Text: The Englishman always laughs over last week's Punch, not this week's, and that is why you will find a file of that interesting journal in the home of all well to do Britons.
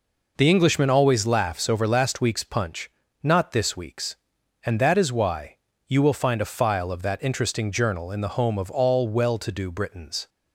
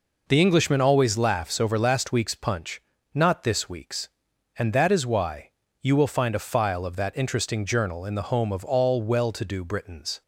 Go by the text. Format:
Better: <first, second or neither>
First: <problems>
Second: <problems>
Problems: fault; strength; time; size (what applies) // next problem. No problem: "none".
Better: neither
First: pauses between "why" and "you"; slight; at 5.5 s; 0.32 s long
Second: pauses between "why" and "you"; slight; at 5.5 s; 0.32 s long